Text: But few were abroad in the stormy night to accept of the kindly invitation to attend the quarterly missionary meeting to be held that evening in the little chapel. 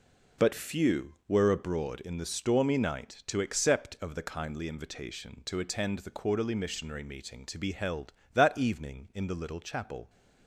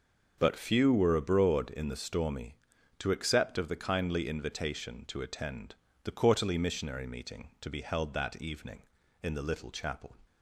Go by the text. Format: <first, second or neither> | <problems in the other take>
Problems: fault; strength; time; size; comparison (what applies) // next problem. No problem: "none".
first | starts louder than the rest; noticeable; until 1.3 s; 6 dB // skips "night"; at 2.7 s // pauses between "attend" and "the"; slight; at 5.7 s; 0.30 s long